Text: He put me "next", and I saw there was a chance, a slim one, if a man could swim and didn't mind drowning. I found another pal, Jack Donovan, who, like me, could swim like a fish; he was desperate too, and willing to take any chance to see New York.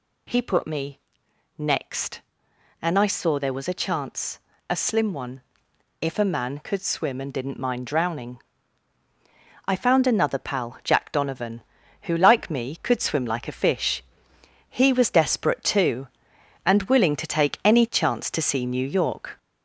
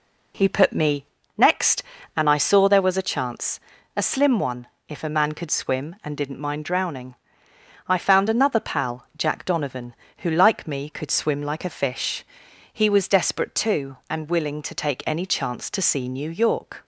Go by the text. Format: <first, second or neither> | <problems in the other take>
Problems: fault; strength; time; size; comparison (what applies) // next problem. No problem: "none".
second | gets louder; noticeable; throughout; 4.5 dB // pauses between "me" and "next"; noticeable; at 0.9 s; 0.58 s long; slight in the second